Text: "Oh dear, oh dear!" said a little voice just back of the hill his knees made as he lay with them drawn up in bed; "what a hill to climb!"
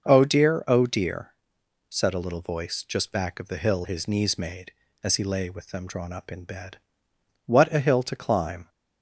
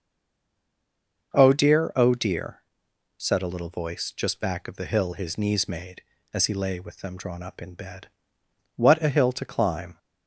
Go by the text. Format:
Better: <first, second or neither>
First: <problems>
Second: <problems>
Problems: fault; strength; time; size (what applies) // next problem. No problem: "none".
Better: first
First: starts louder than the rest; noticeable; until 1.0 s; 6 dB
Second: stays silent before the first word; noticeable; until 1.3 s; 1.3 s long // starts louder than the rest; noticeable; until 2.3 s; 6 dB